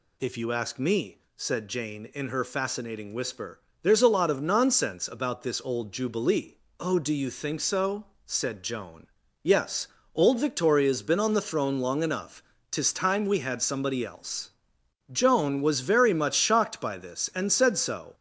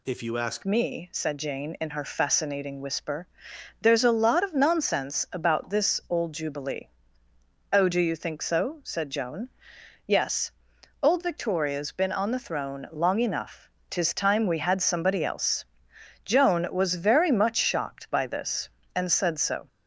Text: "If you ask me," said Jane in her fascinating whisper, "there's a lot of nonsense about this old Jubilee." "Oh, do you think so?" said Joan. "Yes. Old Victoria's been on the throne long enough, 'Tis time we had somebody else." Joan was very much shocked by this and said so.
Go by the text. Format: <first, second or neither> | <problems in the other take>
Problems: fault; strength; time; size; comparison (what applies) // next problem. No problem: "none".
first | changes voice at "me"; from 0.6 s on; 19.0 s long